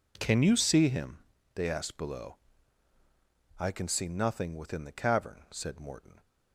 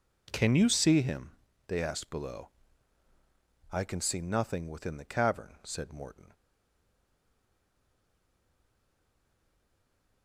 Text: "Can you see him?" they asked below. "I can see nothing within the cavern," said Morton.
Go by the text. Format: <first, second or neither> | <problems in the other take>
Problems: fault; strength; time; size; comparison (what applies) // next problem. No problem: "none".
first | stays silent after the last word; strong; from 6.3 s on; 3.9 s long